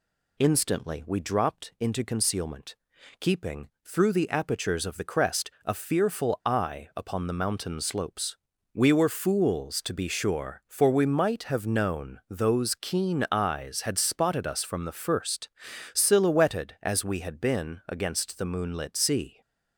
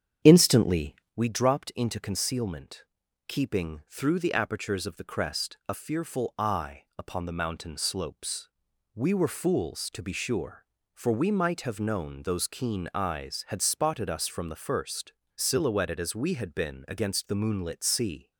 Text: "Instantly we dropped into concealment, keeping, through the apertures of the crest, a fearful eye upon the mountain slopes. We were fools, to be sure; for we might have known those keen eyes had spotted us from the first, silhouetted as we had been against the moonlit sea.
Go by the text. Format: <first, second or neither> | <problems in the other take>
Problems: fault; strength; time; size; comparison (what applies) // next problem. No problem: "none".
first | starts louder than the rest; strong; until 1.2 s; 8.5 dB // pauses between "Instantly" and "we"; slight; at 0.9 s; 0.20 s long